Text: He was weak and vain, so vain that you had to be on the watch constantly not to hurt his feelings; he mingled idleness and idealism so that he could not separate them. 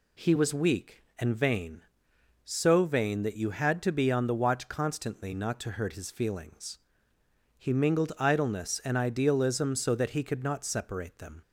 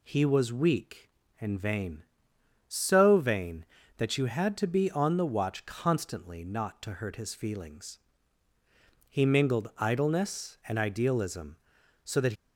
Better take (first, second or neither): first